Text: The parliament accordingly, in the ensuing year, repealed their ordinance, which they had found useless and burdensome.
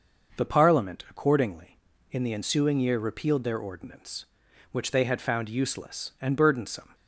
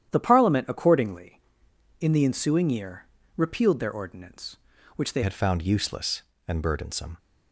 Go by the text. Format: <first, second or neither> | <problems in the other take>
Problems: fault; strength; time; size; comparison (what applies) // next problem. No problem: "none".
first | starts louder than the rest; strong; until 1.1 s; 10 dB; noticeable in the first // changes voice at "had"; from 5.2 s on; 1.9 s long